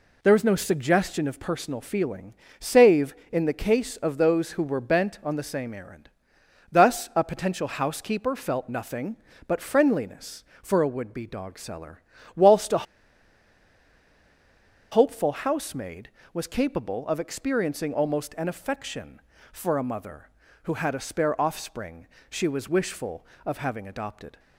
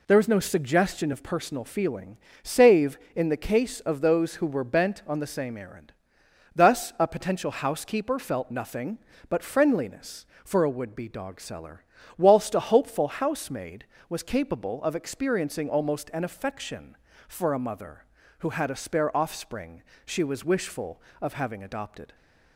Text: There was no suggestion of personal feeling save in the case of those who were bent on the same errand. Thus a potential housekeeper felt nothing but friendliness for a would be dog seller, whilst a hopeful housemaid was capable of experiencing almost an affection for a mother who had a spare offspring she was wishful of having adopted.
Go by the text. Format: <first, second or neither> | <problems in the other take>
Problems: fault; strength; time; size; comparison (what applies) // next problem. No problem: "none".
second | pauses between "feeling" and "save"; slight; at 2.3 s; 0.26 s long; slight in the second // pauses between "a" and "hopeful"; strong; at 12.8 s; 2.0 s long // pauses between "offspring" and "she"; slight; at 22.0 s; 0.24 s long; slight in the second